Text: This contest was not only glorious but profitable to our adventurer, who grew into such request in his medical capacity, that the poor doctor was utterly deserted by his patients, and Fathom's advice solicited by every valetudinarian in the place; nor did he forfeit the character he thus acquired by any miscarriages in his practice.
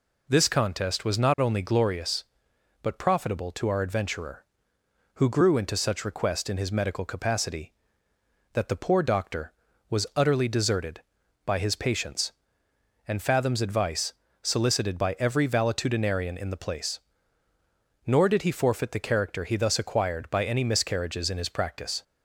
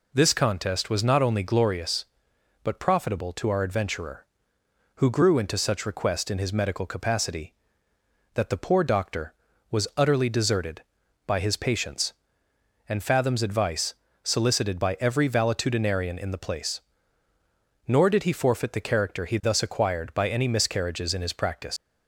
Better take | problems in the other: first | pauses between "advice" and "solicited"; slight; at 13.9 s; 0.30 s long; slight in the first // leaves "practice" unfinished; at 21.7 s; 105 ms

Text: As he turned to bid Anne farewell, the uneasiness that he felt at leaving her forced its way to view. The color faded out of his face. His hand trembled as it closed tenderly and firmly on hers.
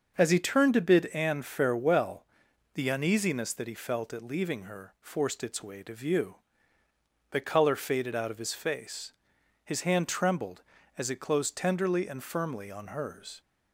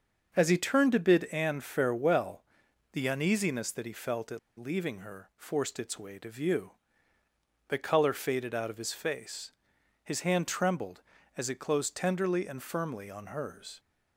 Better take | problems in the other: first | starts louder than the rest; until 1.3 s; 6.5 dB; also in the first // pauses between "at" and "leaving"; slight; at 4.3 s; 0.18 s long

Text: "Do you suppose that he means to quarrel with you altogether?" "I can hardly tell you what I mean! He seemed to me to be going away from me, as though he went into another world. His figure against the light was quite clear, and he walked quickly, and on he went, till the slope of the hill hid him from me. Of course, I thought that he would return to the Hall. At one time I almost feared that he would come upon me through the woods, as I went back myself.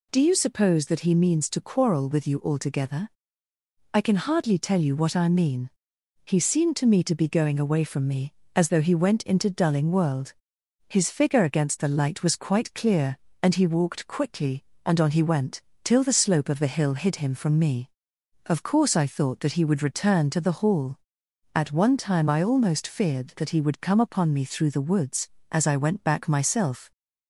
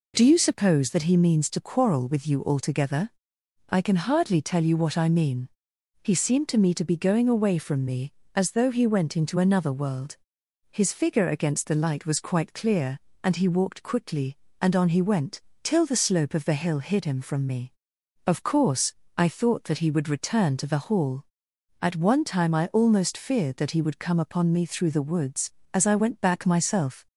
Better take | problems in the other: second | says "dulling" for "another"; at 9.4 s

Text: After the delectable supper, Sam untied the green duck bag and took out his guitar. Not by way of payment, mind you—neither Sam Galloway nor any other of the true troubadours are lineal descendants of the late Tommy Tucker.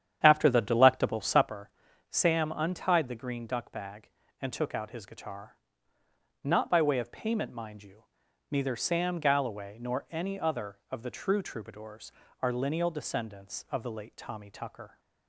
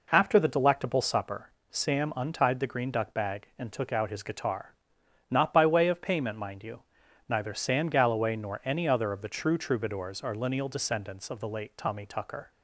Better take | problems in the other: second | starts louder than the rest; strong; until 1.5 s; 9.5 dB

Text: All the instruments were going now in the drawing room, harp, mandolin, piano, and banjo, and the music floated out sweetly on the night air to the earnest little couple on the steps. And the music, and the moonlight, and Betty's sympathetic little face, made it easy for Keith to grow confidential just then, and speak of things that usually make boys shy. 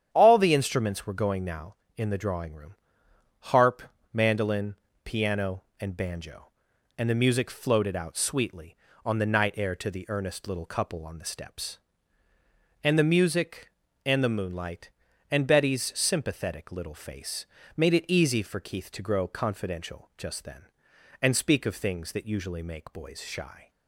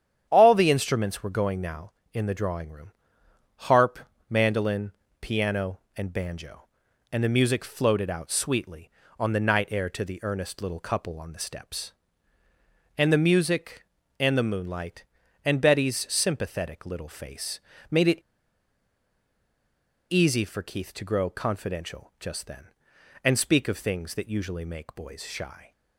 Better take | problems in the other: first | starts louder than the rest; strong; until 1.3 s; 9.5 dB; strong in the first // pauses between "it" and "easy"; strong; at 18.1 s; 1.9 s long

